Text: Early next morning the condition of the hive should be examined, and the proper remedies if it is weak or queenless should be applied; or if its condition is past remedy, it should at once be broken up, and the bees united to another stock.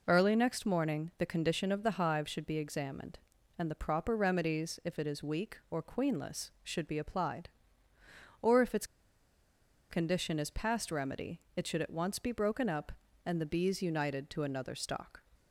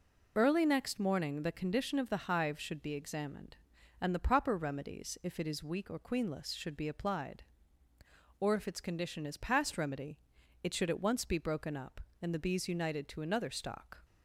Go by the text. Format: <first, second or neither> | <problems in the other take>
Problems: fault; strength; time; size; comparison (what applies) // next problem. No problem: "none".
second | pauses between "its" and "condition"; at 8.8 s; 1.0 s long